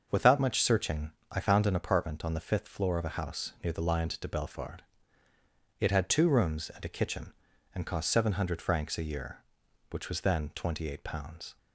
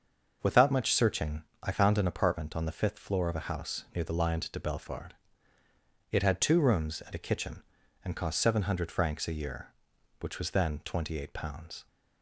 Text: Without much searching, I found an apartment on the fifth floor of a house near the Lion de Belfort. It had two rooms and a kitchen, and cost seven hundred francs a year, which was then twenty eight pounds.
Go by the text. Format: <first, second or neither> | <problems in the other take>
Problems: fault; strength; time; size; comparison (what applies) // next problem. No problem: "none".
neither | starts louder than the rest; the same in both